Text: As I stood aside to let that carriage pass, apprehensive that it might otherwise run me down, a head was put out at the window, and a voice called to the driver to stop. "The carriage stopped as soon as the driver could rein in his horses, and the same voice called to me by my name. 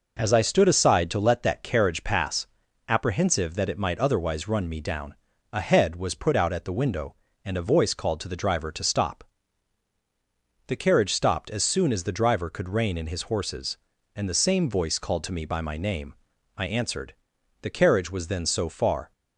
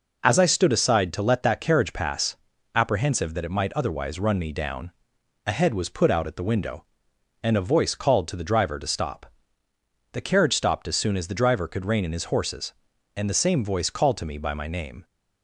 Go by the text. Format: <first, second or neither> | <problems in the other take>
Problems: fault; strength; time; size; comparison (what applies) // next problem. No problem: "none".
second | goes on to say "I answered The carriage was then so far"; strong; from 16.5 s on; 2.5 s long